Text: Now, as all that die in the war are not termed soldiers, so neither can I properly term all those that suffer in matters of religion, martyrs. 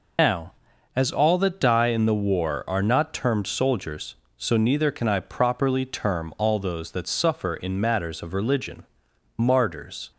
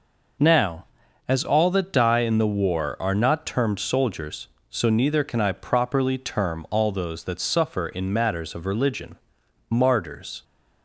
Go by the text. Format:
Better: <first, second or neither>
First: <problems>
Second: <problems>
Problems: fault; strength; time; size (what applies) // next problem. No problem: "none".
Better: second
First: loses the start of "Now"; at 0.1 s; 120 ms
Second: none